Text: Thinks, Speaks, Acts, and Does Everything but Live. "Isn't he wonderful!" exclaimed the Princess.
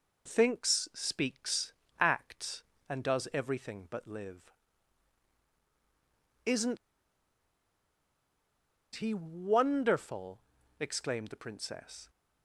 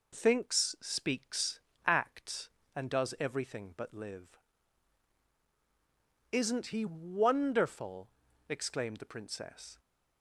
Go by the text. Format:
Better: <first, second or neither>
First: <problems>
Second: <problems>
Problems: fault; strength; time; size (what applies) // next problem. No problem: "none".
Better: second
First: pauses between "Isn't" and "he"; strong; at 6.7 s; 2.1 s long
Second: none